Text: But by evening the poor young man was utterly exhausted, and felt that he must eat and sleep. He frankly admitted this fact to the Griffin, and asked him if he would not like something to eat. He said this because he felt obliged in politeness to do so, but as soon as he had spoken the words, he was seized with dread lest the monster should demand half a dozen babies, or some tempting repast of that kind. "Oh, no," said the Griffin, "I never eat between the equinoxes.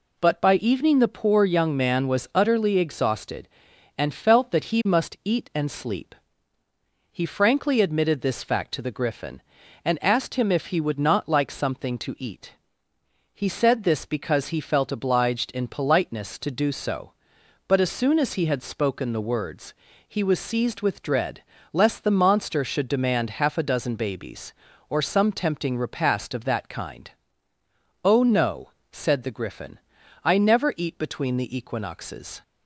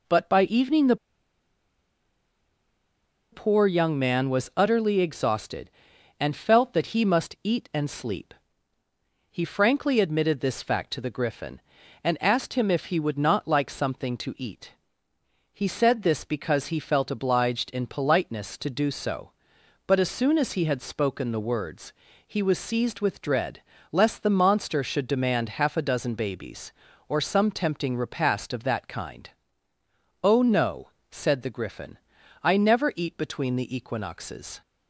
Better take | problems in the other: first | pauses between "the" and "poor"; strong; at 0.9 s; 2.3 s long // pauses between "dread" and "lest"; slight; at 23.6 s; 0.30 s long; slight in the first

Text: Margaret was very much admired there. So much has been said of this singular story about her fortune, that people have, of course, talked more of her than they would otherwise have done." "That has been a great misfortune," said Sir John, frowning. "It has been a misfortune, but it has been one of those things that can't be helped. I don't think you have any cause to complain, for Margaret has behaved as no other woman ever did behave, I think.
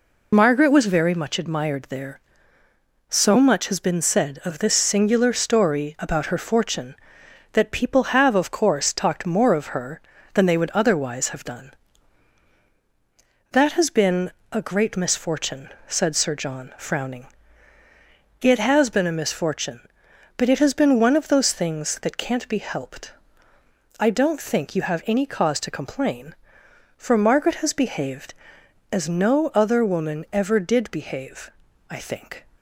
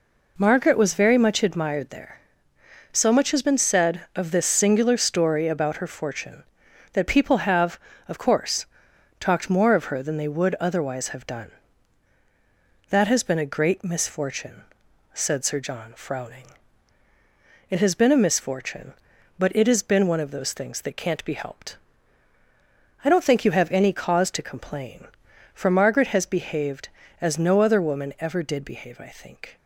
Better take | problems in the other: second | loses the start of "Margaret"; at 0.3 s; 45 ms // pauses between "been" and "a"; slight; at 14.3 s; 0.20 s long

